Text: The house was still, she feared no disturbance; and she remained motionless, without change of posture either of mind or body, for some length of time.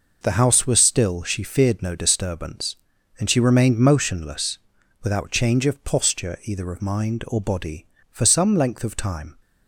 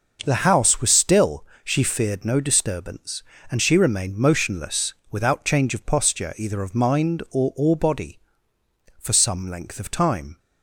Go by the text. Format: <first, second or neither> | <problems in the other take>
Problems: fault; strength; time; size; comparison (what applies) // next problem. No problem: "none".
first | starts louder than the rest; until 1.2 s; 6 dB // says "or" twice; at 7.5 s